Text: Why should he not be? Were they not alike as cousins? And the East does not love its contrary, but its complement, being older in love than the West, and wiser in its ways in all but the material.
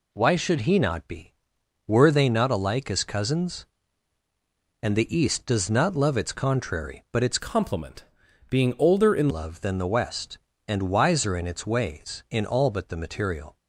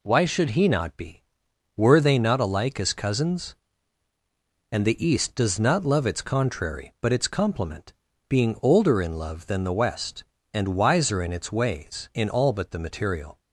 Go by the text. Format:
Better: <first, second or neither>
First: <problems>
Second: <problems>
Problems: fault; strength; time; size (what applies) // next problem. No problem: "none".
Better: second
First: changes voice from "complement" to "in"; from 7.3 to 9.2 s; 1.9 s long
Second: none